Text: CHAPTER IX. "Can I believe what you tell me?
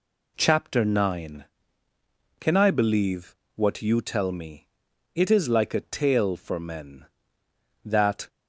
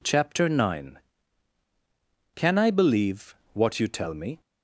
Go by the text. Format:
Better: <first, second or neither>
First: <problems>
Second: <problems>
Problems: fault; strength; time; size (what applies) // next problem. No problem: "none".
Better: second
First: pauses between "believe" and "what"; slight; at 3.3 s; 0.18 s long // goes on to say "It is like a tale for men that"; strong; from 5.1 s on; 3.1 s long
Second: pauses between "believe" and "what"; slight; at 3.3 s; 0.18 s long